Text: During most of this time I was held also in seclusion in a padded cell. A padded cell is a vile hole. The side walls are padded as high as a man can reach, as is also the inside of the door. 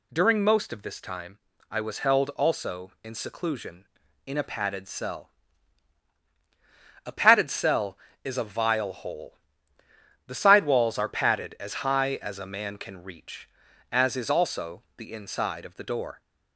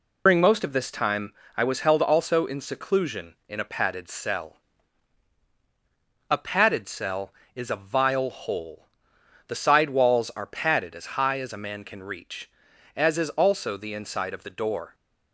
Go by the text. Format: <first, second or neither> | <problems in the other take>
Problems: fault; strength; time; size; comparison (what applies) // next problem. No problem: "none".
first | loses the start of "During"; at 0.2 s; 110 ms // pauses between "time" and "I"; slight; at 1.3 s; 0.24 s long; slight in the first